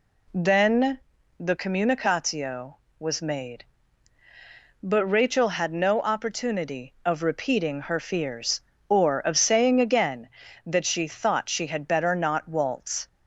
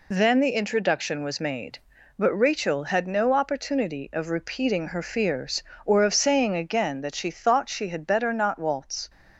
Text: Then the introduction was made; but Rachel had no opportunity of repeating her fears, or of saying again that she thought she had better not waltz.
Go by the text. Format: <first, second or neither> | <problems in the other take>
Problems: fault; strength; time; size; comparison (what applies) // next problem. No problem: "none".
second | pauses between "Then" and "the"; at 0.9 s; 0.40 s long // says "communicatio" for "introduction"; at 1.5 s